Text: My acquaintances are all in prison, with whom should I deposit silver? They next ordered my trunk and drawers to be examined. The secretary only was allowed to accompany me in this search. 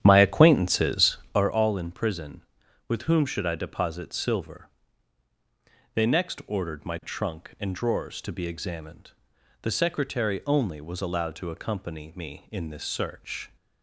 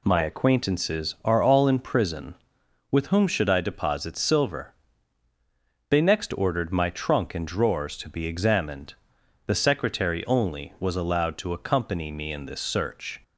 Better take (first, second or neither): second